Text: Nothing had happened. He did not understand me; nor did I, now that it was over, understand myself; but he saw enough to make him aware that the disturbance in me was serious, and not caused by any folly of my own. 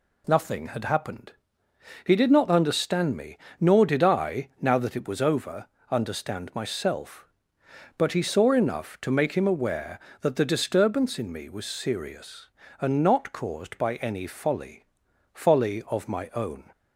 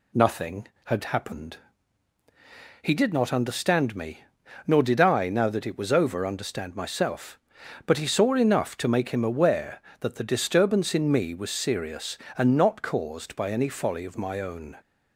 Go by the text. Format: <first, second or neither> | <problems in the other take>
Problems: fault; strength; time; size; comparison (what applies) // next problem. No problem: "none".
second | says "folly" twice; at 15.3 s